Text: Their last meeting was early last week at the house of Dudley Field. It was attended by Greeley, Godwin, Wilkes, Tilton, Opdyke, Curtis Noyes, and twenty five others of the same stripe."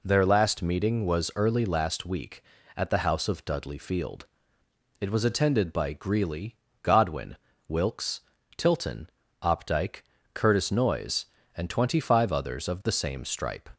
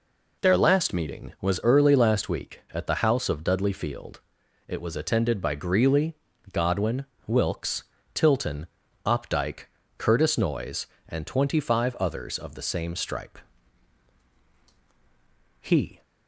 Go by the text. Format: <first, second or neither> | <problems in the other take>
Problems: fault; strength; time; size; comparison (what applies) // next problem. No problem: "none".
first | goes on to say "He"; slight; from 15.5 s on; 0.42 s long